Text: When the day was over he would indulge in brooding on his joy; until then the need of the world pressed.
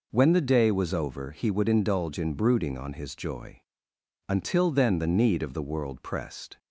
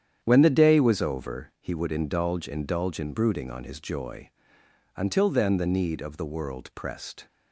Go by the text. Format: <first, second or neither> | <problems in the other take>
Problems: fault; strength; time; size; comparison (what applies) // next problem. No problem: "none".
first | starts louder than the rest; strong; until 1.2 s; 9 dB // says "indulge" twice; at 2.4 s